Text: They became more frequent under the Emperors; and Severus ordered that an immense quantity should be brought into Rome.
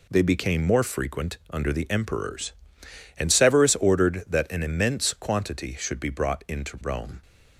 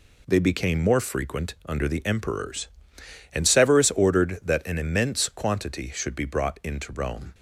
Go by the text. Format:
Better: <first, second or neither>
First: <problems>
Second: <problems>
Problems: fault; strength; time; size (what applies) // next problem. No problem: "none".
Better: neither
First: none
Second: none